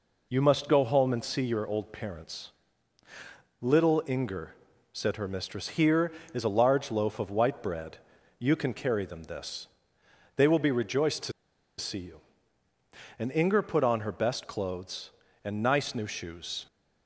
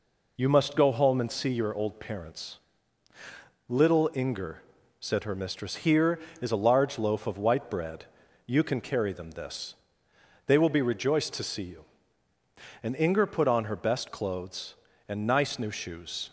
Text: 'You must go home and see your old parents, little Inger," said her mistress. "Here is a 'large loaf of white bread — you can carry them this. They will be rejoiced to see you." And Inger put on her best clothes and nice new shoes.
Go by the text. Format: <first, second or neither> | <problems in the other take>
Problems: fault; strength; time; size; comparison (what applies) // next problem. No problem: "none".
second | pauses between "to" and "see"; noticeable; at 11.3 s; 0.46 s long